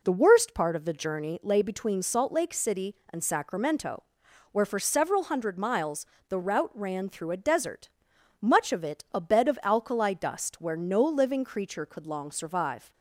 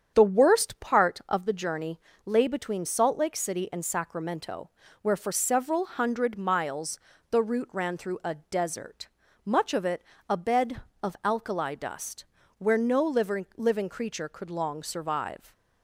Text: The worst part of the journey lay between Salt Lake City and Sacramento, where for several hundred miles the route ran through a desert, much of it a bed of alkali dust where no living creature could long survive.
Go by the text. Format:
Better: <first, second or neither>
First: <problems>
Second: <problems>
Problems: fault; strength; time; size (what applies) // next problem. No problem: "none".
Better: first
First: pauses between "miles" and "the"; slight; at 6.0 s; 0.24 s long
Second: starts louder than the rest; strong; until 1.1 s; 8 dB // pauses between "journey" and "lay"; slight; at 1.9 s; 0.26 s long // pauses between "miles" and "the"; slight; at 6.9 s; 0.30 s long // pauses between "it" and "a"; slight; at 10.0 s; 0.26 s long // pauses between "dust" and "where"; slight; at 12.2 s; 0.32 s long // says "living" twice; at 13.5 s